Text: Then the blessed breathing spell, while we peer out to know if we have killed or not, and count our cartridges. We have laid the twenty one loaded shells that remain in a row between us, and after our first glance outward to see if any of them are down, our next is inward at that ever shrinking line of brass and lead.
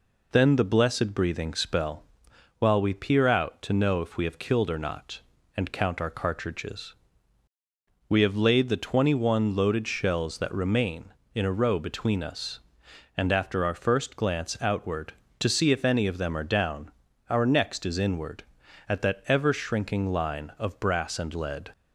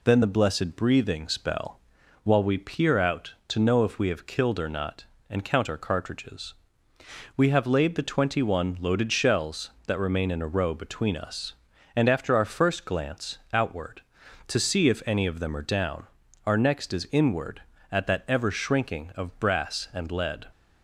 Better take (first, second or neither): first